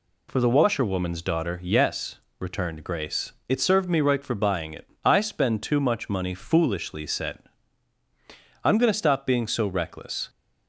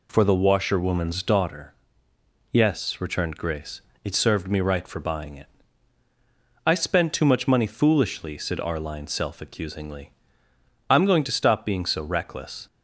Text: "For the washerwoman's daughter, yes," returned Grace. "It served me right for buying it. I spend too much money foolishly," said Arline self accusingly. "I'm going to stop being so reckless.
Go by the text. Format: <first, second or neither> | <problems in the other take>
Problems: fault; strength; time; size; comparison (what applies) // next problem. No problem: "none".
second | skips "Arline self accusingly"; at 8.0 s